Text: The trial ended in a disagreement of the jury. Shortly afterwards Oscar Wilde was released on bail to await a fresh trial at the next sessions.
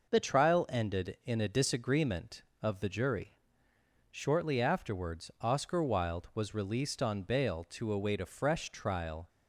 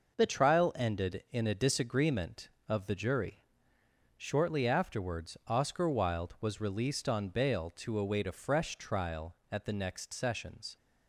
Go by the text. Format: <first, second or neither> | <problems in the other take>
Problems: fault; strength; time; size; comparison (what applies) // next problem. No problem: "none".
second | stops before "at the next sessions"; at 9.2 s